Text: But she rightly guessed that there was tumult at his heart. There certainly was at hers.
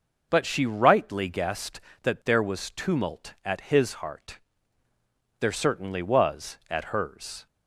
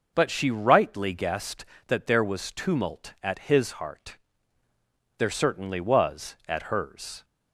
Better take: neither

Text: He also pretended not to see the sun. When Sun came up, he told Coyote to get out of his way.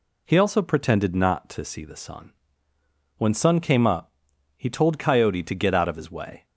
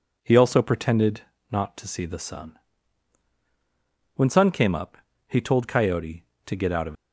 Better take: first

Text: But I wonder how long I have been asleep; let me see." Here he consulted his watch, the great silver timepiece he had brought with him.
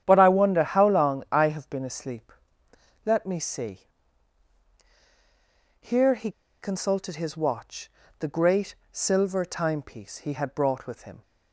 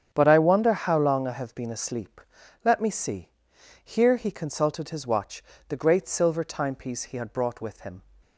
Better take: second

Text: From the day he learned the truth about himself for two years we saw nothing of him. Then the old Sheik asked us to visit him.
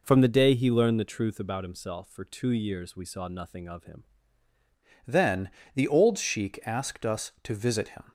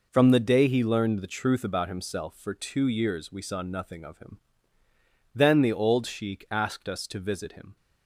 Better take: second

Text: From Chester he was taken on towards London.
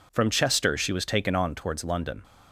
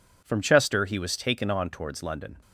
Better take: second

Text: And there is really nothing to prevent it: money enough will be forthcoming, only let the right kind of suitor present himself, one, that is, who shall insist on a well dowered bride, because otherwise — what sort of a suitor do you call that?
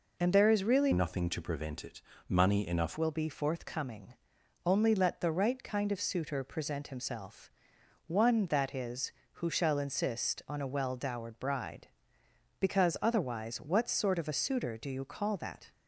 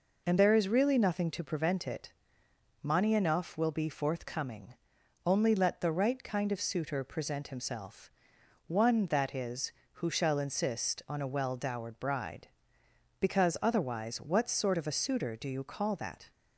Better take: second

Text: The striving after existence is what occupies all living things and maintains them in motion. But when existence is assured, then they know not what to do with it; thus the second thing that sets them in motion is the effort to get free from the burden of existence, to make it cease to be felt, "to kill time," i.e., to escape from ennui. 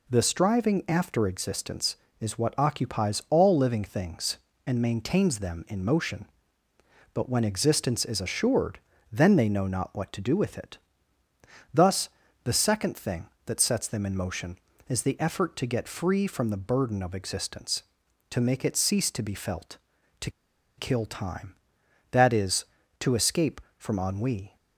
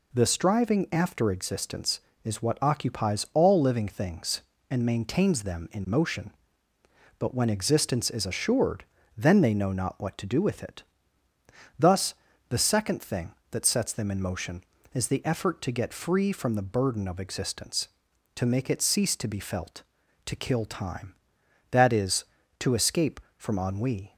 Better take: second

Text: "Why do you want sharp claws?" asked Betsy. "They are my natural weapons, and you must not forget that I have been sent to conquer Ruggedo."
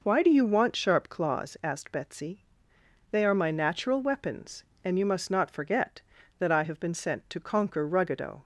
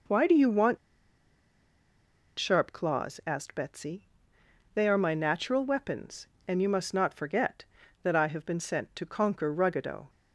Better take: first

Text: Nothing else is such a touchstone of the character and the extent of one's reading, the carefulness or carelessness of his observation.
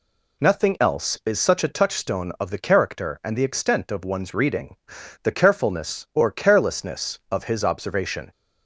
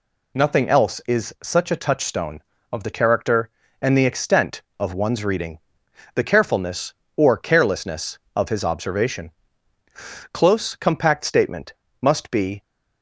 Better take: first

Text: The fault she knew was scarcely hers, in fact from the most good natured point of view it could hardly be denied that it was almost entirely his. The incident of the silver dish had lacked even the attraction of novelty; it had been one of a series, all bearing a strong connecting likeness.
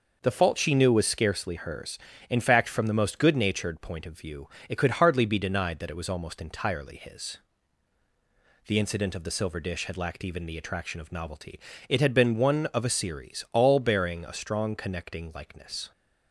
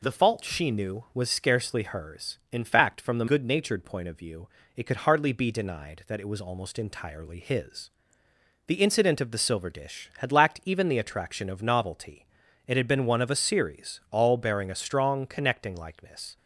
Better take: first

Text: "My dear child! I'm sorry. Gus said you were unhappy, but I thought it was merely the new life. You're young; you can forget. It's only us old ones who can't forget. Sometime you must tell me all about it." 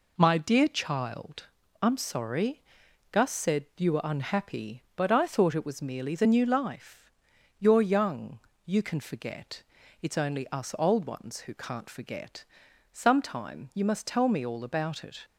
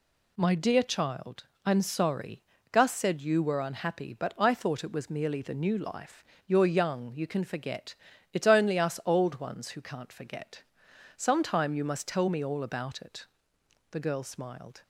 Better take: first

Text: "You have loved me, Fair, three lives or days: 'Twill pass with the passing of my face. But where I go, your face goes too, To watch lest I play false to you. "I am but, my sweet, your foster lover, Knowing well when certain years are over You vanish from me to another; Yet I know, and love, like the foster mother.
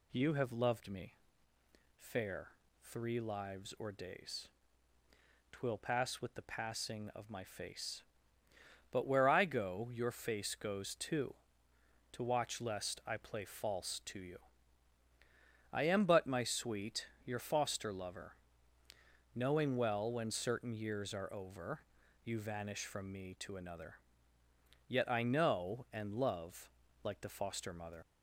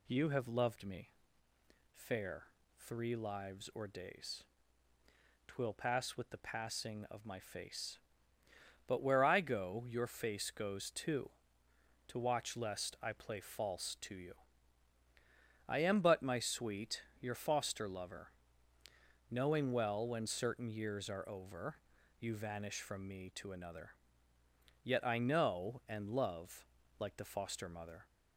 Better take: second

